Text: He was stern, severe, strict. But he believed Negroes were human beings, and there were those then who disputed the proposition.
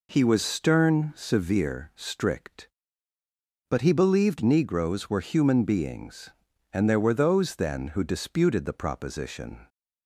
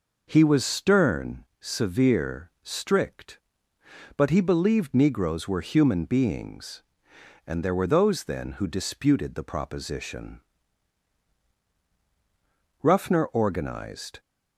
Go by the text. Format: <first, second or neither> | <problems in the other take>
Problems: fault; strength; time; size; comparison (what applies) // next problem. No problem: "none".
first | goes on to say "Ruffner organized"; from 12.8 s on; 1.3 s long